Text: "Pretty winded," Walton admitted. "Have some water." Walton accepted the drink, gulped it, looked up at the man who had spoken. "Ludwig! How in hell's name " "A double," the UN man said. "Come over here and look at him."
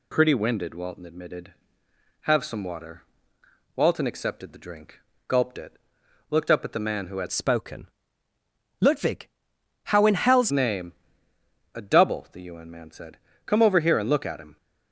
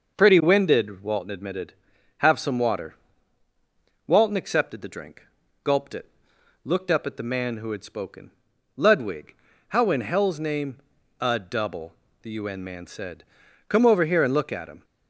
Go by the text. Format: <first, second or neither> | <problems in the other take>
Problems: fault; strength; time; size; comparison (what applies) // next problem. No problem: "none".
second | changes voice from "spoken" to "hell's"; from 7.3 to 10.5 s; 3.2 s long